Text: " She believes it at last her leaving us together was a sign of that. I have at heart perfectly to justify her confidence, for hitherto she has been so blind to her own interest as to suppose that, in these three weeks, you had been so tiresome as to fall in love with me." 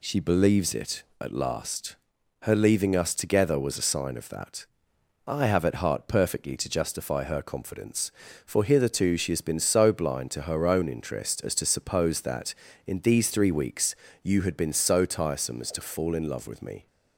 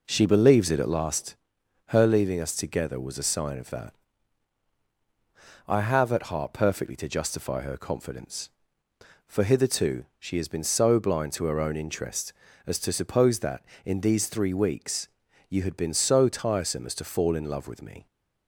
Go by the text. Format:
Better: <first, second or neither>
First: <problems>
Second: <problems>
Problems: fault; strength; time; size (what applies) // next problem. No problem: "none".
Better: first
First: pauses between "last" and "her"; noticeable; at 1.9 s; 0.48 s long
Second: starts louder than the rest; noticeable; until 1.0 s; 4.5 dB // pauses between "last" and "her"; noticeable; at 1.3 s; 0.54 s long